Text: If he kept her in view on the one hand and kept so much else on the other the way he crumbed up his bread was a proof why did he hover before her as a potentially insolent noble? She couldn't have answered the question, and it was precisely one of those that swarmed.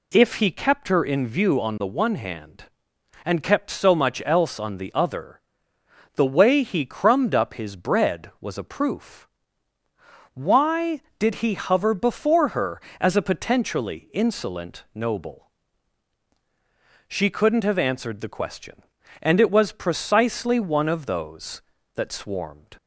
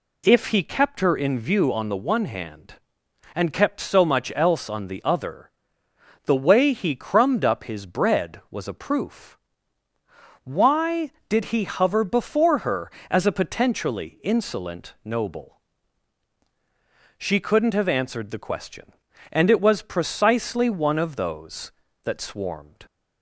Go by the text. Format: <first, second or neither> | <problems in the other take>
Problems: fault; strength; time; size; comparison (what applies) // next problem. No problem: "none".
neither | pauses between "other" and "the"; noticeable; the same in both // pauses between "proof" and "why"; the same in both